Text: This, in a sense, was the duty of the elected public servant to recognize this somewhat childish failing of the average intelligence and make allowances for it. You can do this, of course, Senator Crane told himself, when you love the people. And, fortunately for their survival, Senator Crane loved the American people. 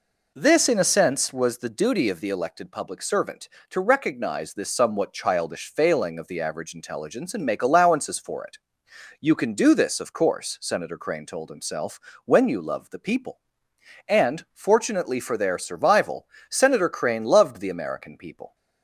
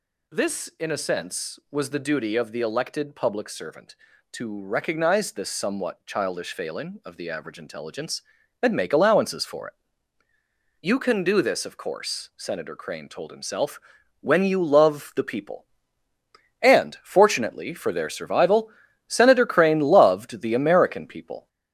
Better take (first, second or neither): first